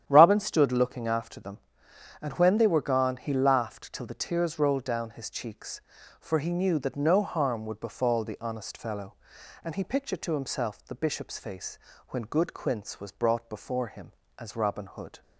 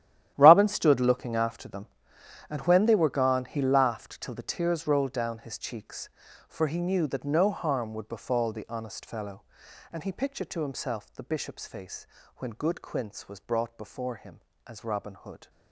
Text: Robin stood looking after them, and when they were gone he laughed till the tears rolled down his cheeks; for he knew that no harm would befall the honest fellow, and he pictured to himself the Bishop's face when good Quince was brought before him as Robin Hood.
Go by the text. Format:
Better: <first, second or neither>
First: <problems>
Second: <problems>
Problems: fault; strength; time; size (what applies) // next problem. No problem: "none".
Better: first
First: starts louder than the rest; strong; until 1.0 s; 10 dB // pauses between "face" and "when"; slight; at 11.7 s; 0.30 s long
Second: gets quieter; strong; throughout; 15.5 dB // starts louder than the rest; strong; until 1.3 s; 12 dB // pauses between "face" and "when"; slight; at 12.0 s; 0.30 s long